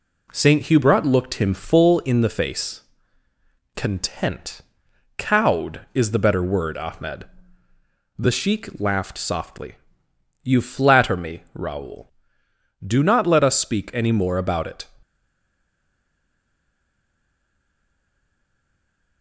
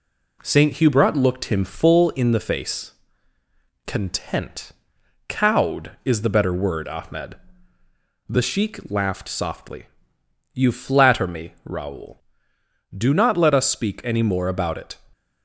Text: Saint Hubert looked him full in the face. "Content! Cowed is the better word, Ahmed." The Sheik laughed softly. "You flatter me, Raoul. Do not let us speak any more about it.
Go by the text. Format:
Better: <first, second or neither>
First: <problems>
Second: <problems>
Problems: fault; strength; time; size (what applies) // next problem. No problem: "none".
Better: second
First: stays silent after the last word; strong; from 15.0 s on; 4.2 s long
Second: none